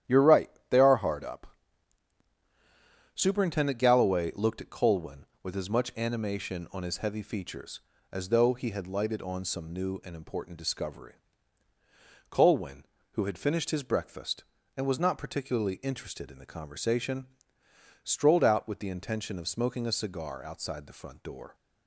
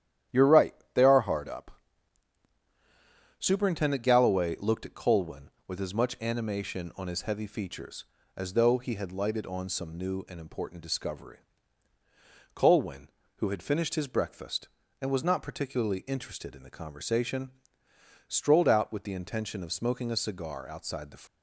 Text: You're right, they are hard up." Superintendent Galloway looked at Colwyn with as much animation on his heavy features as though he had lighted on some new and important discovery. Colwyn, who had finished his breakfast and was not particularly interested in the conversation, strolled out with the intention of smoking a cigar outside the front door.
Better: first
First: starts louder than the rest; strong; until 1.2 s; 11.5 dB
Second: starts louder than the rest; strong; until 1.5 s; 11.5 dB // stops before "front door"; at 21.2 s

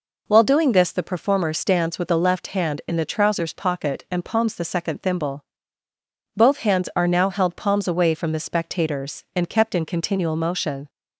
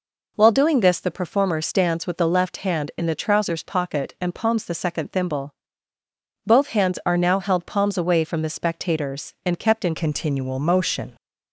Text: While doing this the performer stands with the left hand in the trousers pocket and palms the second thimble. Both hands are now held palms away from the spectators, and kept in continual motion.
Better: first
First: none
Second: changes voice at "continual"; from 9.9 s on; 1.2 s long

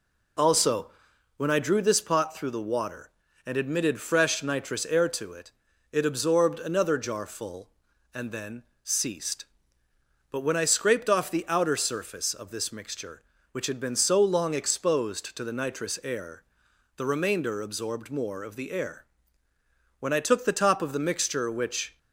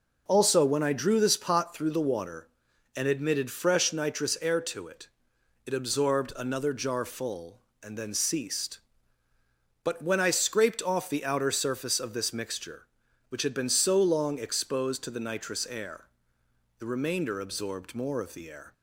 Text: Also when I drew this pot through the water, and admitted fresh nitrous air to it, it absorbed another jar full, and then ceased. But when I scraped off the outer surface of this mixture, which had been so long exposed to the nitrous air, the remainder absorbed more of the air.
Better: second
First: pauses between "Also" and "when"; noticeable; at 0.8 s; 0.46 s long // pauses between "then" and "ceased"; slight; at 8.6 s; 0.18 s long // goes on to say "When I took the top of the mixture which"; strong; from 19.9 s on; 1.9 s long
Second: none

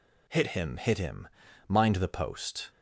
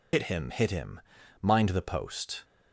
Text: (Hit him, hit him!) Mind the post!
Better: first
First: none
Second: loses the start of "Hit"; at 0.1 s; 85 ms

